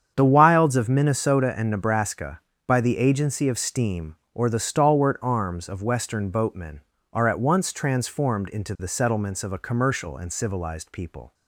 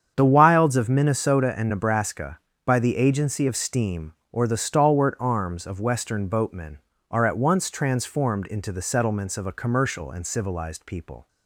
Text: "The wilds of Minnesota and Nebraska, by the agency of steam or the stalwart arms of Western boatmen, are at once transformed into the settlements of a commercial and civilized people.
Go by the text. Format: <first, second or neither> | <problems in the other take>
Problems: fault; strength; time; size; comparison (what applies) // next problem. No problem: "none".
neither | starts louder than the rest; strong; the same in both